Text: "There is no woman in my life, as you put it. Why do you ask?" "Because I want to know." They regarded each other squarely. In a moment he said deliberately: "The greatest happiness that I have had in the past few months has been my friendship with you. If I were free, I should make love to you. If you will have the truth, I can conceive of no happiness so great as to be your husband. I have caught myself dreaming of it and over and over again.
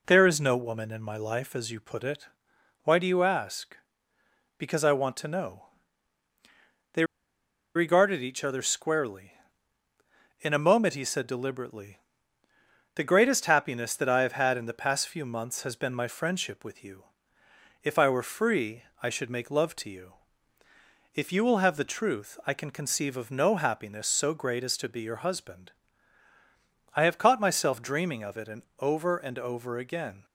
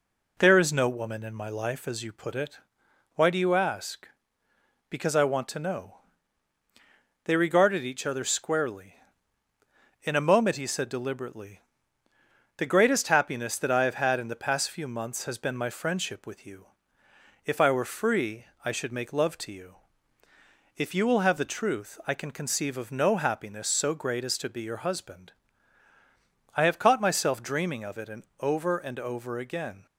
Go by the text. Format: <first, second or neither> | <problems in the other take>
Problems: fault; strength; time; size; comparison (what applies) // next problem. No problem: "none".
second | pauses between "They" and "regarded"; noticeable; at 7.0 s; 0.71 s long // pauses between "and" and "over"; slight; at 28.6 s; 0.18 s long; slight in the second